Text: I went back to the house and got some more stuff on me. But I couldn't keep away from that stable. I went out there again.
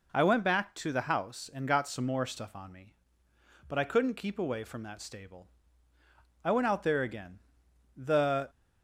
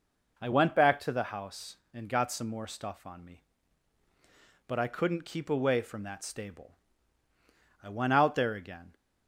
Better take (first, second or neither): second